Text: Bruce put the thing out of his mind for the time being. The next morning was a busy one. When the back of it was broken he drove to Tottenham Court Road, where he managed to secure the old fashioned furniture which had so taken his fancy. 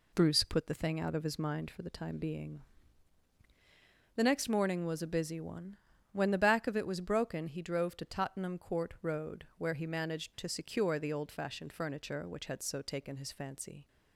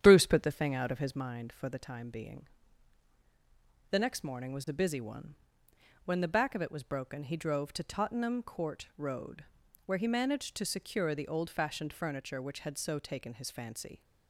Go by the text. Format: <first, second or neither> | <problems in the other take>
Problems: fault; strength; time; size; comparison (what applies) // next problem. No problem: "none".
first | starts louder than the rest; strong; until 1.2 s; 9.5 dB